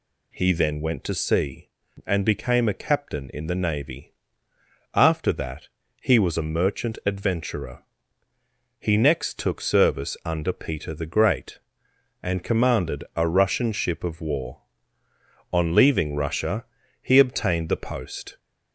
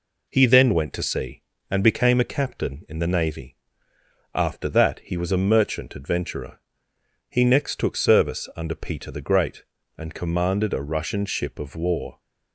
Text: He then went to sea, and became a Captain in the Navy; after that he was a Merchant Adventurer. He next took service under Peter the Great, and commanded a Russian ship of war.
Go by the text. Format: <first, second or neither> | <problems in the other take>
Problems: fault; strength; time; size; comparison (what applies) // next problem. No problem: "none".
second | pauses between "that" and "he"; slight; at 5.6 s; 0.32 s long // goes on to say "On leaving Russia he obtained the post"; strong; from 15.5 s on; 2.8 s long